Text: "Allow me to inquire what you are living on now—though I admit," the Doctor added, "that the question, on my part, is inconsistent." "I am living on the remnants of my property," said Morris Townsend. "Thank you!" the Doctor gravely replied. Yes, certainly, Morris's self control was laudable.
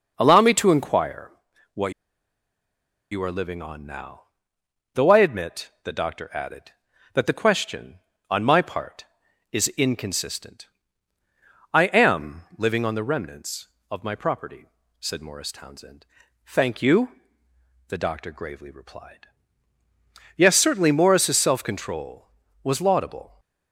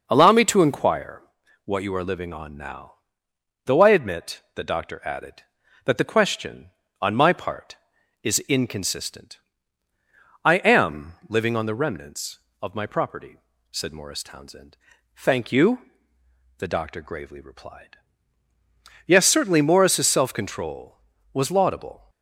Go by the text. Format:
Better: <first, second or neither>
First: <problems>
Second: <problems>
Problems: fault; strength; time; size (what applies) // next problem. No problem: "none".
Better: second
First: pauses between "inquire" and "what"; at 1.3 s; 0.42 s long // pauses between "what" and "you"; at 1.9 s; 1.1 s long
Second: pauses between "inquire" and "what"; at 1.2 s; 0.42 s long